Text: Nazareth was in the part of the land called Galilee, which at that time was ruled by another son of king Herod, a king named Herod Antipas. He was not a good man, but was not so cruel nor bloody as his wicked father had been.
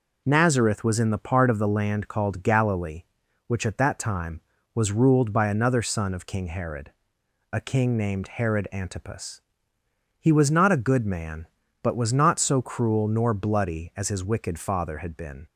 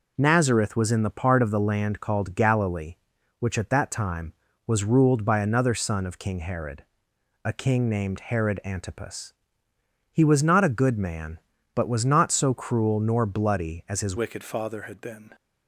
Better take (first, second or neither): first